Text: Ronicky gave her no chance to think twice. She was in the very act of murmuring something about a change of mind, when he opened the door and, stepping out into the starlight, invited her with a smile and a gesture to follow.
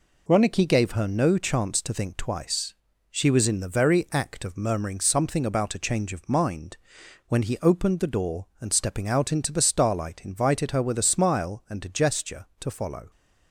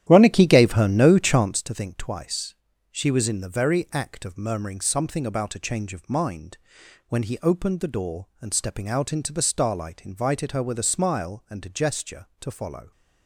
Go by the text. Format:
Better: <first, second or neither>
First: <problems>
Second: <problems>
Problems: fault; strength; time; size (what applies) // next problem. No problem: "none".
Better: first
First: none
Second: starts louder than the rest; strong; until 1.6 s; 11.5 dB